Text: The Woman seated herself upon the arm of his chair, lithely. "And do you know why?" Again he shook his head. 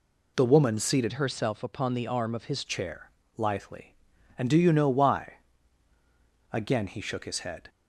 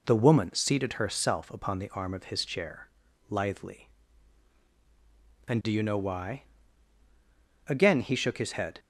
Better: second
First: changes voice from "herself" to "his"; from 1.1 to 2.6 s; 1.5 s long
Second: none

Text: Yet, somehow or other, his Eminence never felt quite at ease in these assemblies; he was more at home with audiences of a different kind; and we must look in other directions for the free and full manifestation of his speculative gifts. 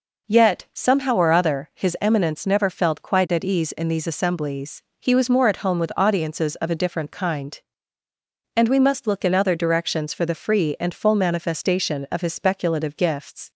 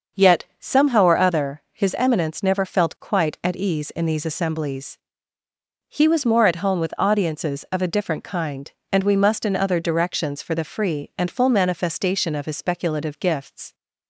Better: first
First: none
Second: starts louder than the rest; until 1.3 s; 6.5 dB // skips "look"; at 9.4 s

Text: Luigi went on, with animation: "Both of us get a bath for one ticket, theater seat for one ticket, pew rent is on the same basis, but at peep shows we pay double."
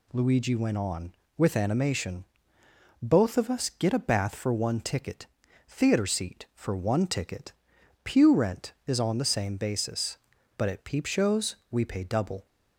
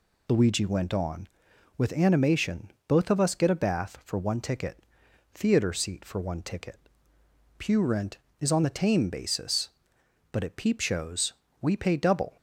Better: first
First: none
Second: says "tame" for "same"; at 8.7 s // pauses between "shows" and "we"; slight; at 11.3 s; 0.28 s long

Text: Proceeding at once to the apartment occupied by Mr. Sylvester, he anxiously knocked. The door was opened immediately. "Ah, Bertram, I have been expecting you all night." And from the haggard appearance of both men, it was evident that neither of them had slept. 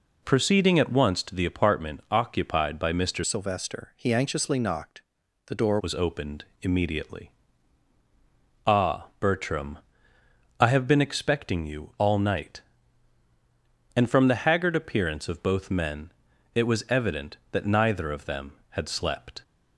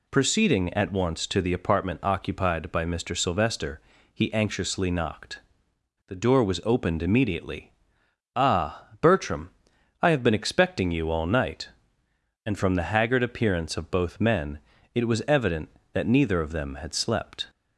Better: second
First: changes voice from "Sylvester" to "door"; from 3.2 to 5.7 s; 2.5 s long // pauses between "opened" and "immediately"; slight; at 6.4 s; 0.16 s long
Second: none

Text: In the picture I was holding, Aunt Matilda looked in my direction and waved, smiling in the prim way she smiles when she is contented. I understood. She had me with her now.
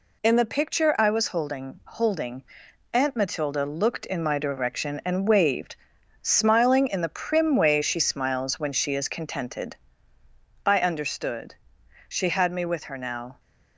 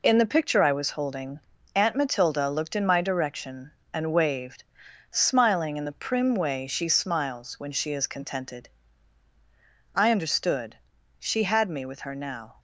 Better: second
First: says "holding" twice; at 1.8 s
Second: none

